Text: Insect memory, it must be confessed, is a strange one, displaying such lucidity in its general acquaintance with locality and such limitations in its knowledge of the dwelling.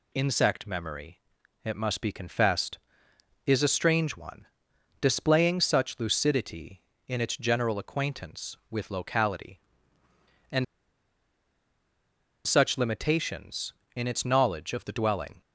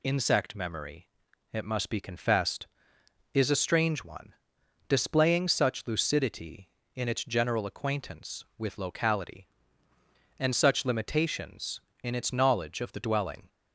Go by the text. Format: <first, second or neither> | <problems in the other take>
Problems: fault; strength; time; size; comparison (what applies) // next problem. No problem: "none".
second | pauses between "and" and "such"; strong; at 10.6 s; 1.8 s long